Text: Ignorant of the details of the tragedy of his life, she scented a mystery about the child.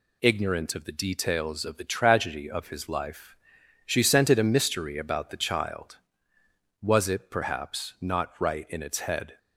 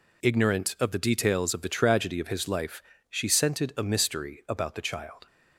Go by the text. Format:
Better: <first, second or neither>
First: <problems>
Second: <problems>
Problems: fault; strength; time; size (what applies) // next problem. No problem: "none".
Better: second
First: goes on to say "Was it perhaps not right in its head"; strong; from 6.8 s on; 2.5 s long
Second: none